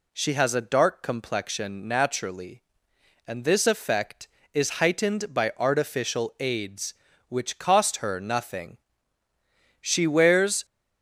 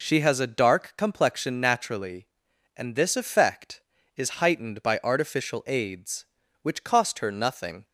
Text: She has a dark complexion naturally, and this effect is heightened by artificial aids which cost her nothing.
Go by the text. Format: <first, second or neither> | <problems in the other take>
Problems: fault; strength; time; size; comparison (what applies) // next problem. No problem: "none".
second | goes on to say "She wears"; noticeable; from 9.8 s on; 0.84 s long